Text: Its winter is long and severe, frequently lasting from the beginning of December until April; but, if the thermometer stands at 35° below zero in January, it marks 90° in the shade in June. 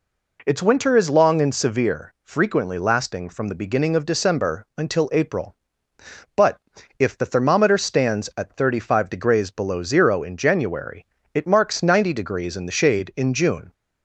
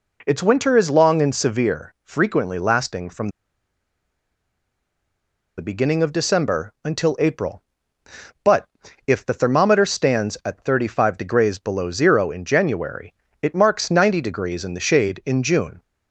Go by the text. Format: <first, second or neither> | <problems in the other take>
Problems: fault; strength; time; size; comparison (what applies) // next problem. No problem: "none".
first | pauses between "from" and "the"; strong; at 3.2 s; 2.2 s long